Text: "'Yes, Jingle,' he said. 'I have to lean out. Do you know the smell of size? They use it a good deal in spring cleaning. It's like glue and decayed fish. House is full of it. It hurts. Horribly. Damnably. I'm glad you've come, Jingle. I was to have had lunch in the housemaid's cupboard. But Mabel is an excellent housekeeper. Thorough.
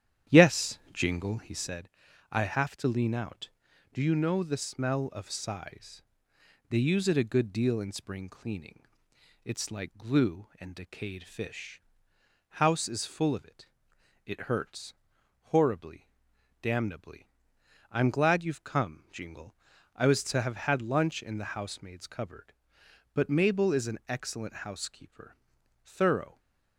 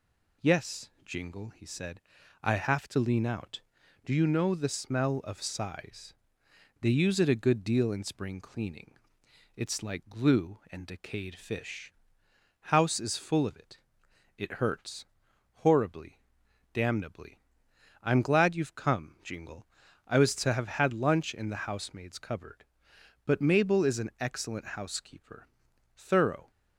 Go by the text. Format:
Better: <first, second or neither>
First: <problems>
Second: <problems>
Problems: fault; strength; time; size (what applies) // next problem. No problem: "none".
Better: second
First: starts louder than the rest; strong; until 1.8 s; 10.5 dB // stays silent after the last word; slight; from 26.2 s on; 0.5 s long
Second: none